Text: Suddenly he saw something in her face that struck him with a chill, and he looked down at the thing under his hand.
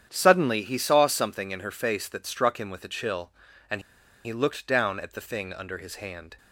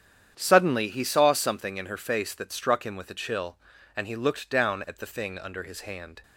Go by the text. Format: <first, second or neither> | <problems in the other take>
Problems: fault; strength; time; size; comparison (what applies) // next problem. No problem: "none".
second | starts louder than the rest; strong; until 1.1 s; 9 dB; strong in the second // pauses between "and" and "he"; at 3.7 s; 0.45 s long